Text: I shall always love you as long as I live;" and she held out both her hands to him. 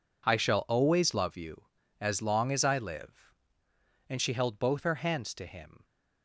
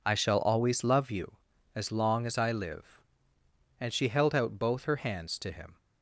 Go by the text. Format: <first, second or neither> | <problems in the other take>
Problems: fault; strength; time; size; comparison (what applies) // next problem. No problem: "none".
second | skips "out"; at 4.5 s